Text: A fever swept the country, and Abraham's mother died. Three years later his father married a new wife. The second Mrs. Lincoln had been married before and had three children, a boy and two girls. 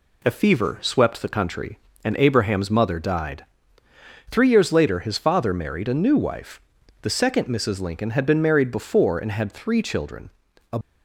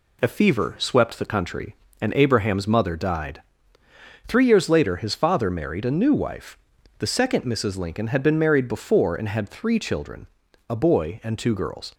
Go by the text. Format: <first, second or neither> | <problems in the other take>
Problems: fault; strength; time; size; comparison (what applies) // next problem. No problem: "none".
second | stops before "boy and two girls"; at 10.8 s